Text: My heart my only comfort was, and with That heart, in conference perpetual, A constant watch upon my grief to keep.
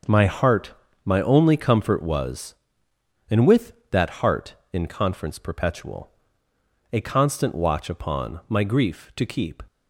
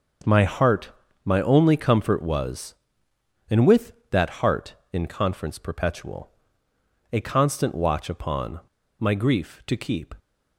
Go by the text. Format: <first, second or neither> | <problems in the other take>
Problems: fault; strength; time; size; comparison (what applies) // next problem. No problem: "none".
first | starts louder than the rest; until 1.5 s; 6 dB; also in the first // pauses between "heart" and "my"; slight; at 0.9 s; 0.34 s long; slight in the first // pauses between "upon" and "my"; at 8.6 s; 0.38 s long